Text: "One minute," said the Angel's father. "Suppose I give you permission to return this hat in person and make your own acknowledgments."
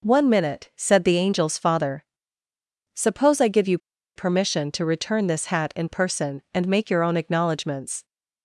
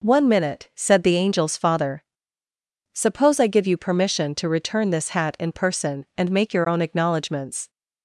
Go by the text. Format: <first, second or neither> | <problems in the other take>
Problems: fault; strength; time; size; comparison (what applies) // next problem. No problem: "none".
second | pauses between "you" and "permission"; at 3.7 s; 0.38 s long